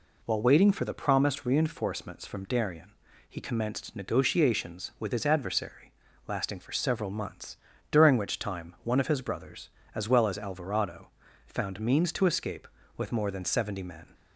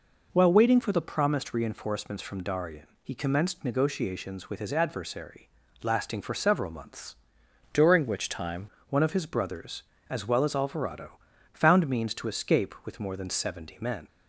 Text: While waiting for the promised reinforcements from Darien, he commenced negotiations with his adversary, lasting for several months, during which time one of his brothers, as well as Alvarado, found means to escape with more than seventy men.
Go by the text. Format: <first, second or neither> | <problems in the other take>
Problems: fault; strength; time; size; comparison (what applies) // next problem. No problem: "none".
first | changes voice from "during" to "time"; from 7.7 to 8.6 s; 0.9 s long